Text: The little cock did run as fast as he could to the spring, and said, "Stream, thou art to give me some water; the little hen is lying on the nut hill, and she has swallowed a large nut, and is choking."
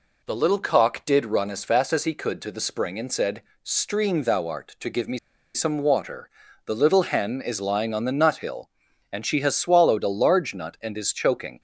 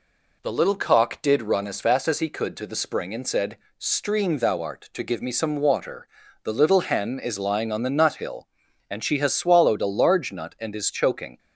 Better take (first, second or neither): second